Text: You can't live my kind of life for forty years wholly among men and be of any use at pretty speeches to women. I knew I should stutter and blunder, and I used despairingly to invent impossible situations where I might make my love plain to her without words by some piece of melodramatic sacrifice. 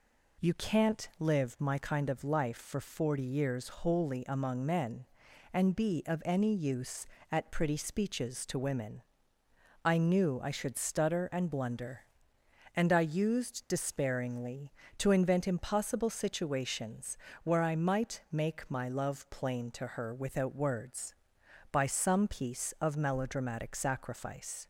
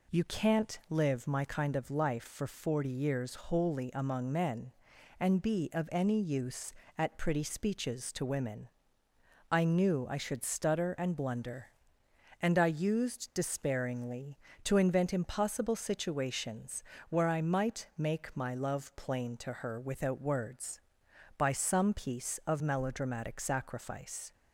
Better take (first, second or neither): neither